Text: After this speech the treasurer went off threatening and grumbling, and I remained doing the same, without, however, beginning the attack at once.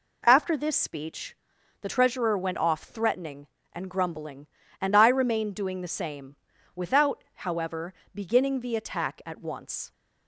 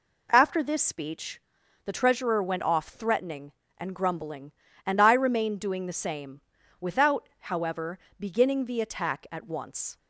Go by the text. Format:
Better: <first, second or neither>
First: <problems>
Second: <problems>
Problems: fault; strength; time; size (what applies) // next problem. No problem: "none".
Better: neither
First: pauses between "speech" and "the"; noticeable; at 1.3 s; 0.46 s long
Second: pauses between "speech" and "the"; at 1.4 s; 0.45 s long